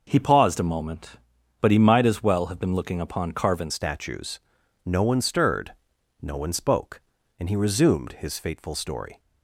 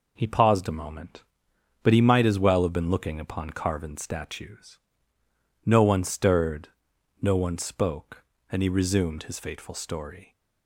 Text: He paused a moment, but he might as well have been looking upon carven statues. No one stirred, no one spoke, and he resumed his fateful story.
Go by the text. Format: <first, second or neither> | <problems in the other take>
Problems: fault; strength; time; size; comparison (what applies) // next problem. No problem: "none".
second | changes voice at "statues"; from 3.6 s on; 5.5 s long